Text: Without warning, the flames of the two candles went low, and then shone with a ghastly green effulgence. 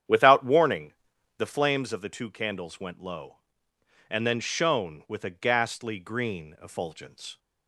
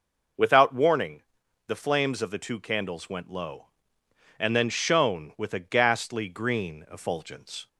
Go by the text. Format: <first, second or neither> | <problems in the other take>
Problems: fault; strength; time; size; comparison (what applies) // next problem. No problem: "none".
second | starts louder than the rest; strong; until 1.9 s; 9 dB